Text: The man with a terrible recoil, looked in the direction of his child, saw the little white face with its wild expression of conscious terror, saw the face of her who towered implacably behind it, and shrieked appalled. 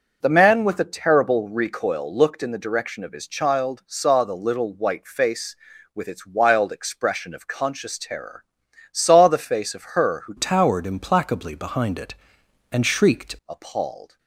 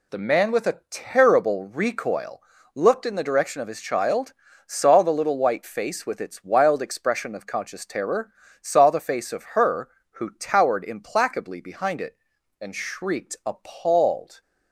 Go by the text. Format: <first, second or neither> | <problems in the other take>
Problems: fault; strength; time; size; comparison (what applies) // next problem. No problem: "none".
second | changes voice from "towered" to "shrieked"; from 10.3 to 13.3 s; 3.0 s long